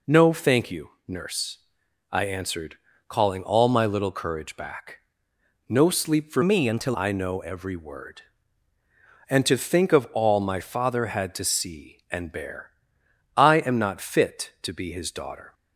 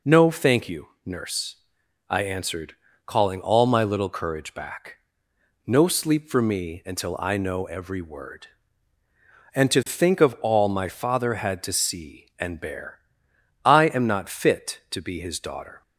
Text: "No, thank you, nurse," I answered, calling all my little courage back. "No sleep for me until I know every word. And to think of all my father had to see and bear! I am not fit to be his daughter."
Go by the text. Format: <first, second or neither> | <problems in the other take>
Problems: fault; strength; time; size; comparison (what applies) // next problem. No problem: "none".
second | changes voice from "me" to "until"; from 6.4 to 6.9 s; 0.5 s long